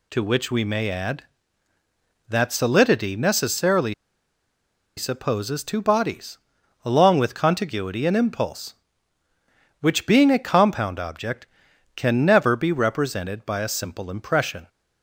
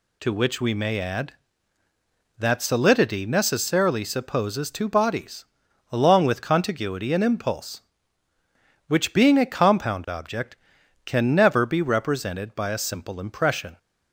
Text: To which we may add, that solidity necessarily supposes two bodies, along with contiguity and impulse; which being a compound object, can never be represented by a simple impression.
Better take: second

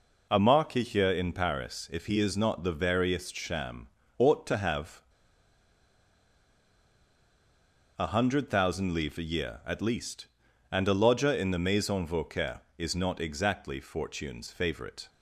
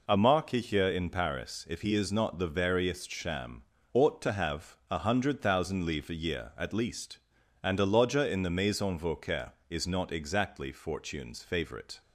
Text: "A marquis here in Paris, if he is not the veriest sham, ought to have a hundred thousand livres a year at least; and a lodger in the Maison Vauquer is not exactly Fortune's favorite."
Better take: second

